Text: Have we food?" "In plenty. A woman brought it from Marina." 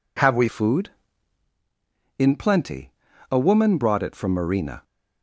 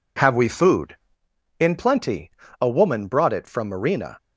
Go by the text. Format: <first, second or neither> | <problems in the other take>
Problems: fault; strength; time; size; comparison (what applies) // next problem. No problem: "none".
second | changes voice at "food"; from 0.4 s on; 4.4 s long